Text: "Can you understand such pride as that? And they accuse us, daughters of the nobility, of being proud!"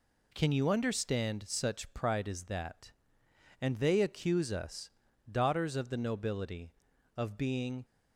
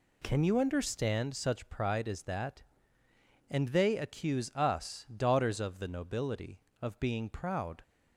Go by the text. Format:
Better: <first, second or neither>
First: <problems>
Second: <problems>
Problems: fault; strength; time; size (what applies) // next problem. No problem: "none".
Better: second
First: stops before "proud"; at 7.8 s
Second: none